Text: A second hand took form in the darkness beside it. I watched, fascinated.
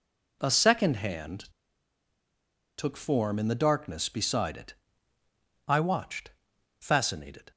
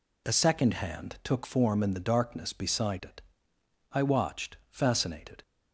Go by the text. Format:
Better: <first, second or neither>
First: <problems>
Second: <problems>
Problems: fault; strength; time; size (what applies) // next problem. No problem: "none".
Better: second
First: pauses between "hand" and "took"; strong; at 1.4 s; 1.3 s long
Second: none